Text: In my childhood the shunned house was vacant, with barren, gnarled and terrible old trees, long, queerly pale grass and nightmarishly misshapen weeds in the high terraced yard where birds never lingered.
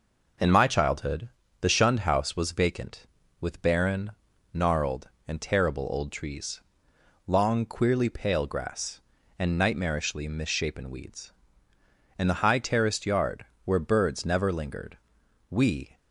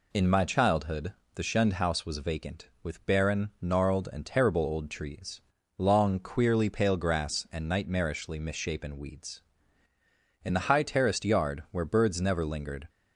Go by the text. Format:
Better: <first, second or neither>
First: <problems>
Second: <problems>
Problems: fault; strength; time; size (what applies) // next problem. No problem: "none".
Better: second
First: pauses between "childhood" and "the"; slight; at 1.2 s; 0.30 s long // pauses between "yard" and "where"; slight; at 13.4 s; 0.20 s long // goes on to say "We"; slight; from 15.5 s on; 0.46 s long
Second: pauses between "childhood" and "the"; slight; at 1.1 s; 0.22 s long